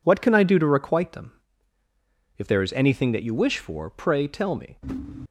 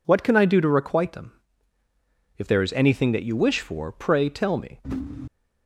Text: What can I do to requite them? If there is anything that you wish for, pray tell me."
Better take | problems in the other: second | gets quieter; strong; throughout; 9.5 dB

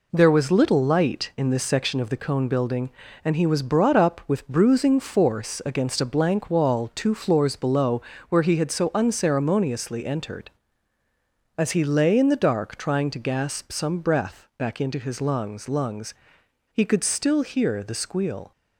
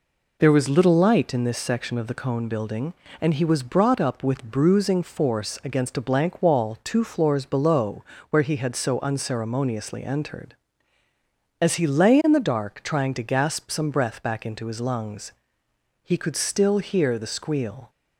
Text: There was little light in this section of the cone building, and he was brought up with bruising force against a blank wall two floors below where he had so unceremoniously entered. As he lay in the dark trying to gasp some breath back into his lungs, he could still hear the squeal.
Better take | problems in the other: second | pauses between "below" and "where"; slight; at 7.9 s; 0.30 s long; slight in the second // says "lungs" twice; at 15.6 s

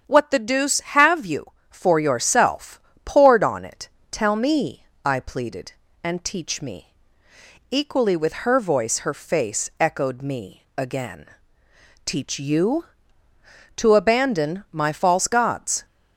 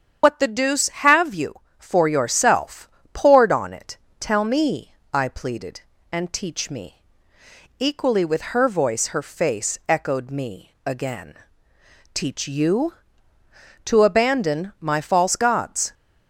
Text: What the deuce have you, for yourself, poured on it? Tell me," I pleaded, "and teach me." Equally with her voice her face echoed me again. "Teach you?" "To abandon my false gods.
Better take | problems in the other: first | loses the start of "What"; at 0.2 s; 80 ms // starts louder than the rest; strong; until 1.2 s; 8 dB; strong in the first

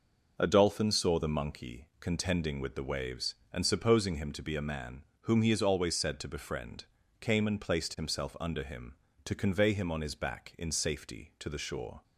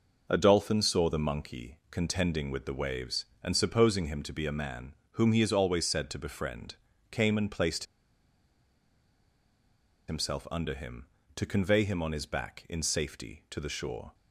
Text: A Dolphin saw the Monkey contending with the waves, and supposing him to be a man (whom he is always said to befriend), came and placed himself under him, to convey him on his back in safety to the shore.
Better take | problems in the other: first | pauses between "placed" and "himself"; strong; at 7.8 s; 2.2 s long

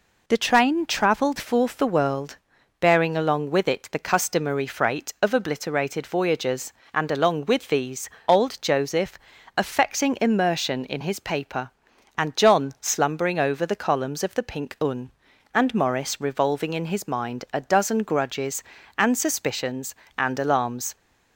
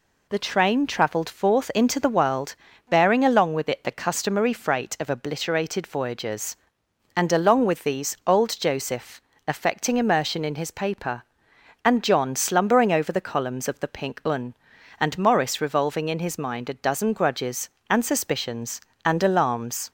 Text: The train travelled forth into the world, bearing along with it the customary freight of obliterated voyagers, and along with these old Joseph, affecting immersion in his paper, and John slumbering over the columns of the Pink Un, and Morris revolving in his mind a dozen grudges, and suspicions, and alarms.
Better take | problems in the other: second | skips "into"; at 1.7 s // pauses between "these" and "old"; slight; at 8.0 s; 0.18 s long

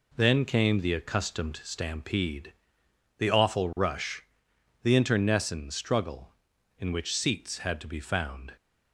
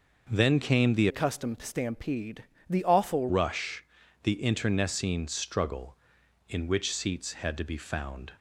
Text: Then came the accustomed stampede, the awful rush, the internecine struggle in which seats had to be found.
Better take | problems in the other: first | changes voice from "accustomed" to "awful"; from 1.0 to 3.2 s; 2.2 s long

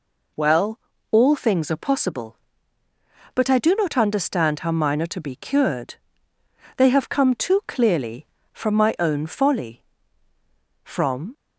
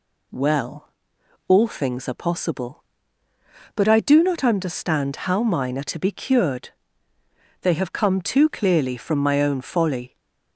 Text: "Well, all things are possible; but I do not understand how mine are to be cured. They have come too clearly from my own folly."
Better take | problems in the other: second | goes on to say "From"; from 10.8 s on; 0.52 s long

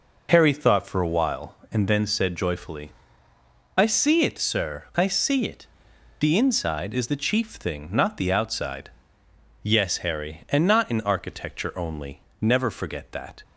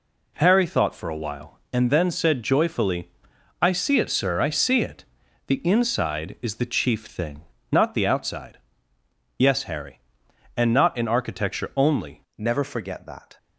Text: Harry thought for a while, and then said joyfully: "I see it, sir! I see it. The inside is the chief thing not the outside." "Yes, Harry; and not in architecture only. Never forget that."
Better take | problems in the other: first | pauses between "thing" and "not"; slight; at 7.4 s; 0.28 s long // changes voice at "Never"; from 12.3 s on; 1.0 s long

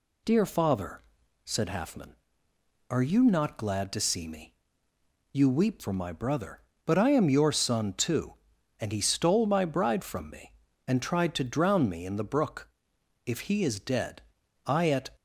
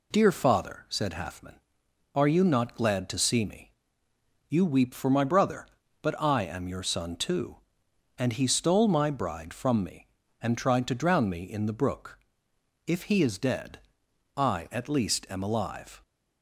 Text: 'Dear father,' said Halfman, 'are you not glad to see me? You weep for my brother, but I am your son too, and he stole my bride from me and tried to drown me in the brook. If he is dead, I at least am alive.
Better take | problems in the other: second | stops before "least am alive"; at 15.1 s

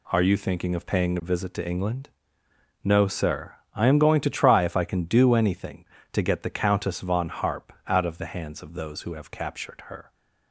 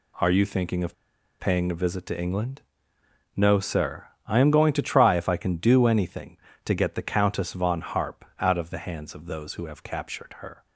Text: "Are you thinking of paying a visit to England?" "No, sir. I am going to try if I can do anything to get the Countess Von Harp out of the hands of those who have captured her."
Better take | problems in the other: first | pauses between "of" and "paying"; at 0.9 s; 0.45 s long

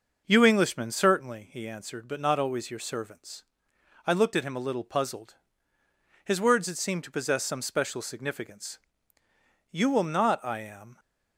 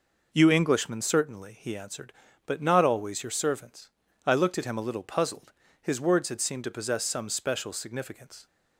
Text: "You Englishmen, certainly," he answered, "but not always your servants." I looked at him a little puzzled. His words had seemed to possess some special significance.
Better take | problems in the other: second | goes on to say "You will not I am"; noticeable; from 9.7 s on; 1.2 s long

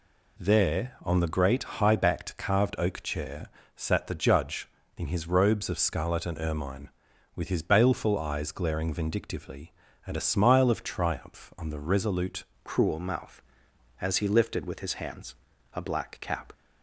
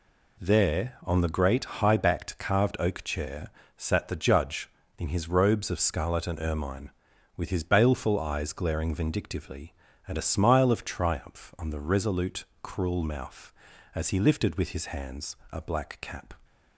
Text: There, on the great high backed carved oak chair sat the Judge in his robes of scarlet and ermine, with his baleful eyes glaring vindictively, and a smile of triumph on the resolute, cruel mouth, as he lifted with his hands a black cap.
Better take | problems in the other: second | pauses between "chair" and "sat"; slight; at 3.4 s; 0.28 s long; slight in the second // changes voice at "cruel"; from 12.6 s on; 3.9 s long // pauses between "hands" and "a"; at 15.3 s; 0.40 s long; slight in the second

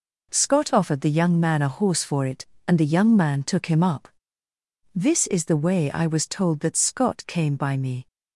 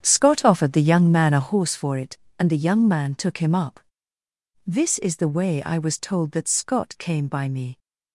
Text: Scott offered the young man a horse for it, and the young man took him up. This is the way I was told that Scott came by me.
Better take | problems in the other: first | starts louder than the rest; strong; until 1.6 s; 9 dB

